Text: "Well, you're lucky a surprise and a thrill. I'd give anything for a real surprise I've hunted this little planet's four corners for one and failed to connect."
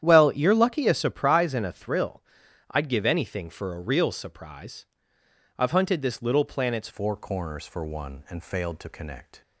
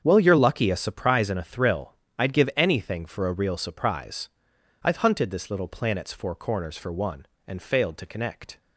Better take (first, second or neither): second